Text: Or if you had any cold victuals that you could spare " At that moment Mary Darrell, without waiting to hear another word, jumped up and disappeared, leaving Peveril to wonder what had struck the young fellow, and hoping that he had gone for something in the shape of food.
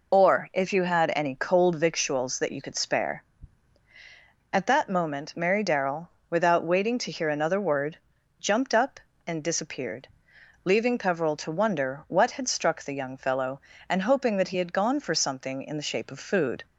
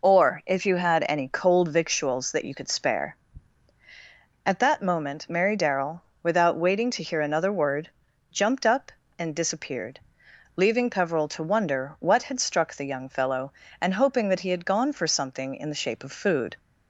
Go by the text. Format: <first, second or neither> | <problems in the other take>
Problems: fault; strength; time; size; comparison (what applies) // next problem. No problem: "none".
second | loses the start of "Or"; at 0.1 s; 25 ms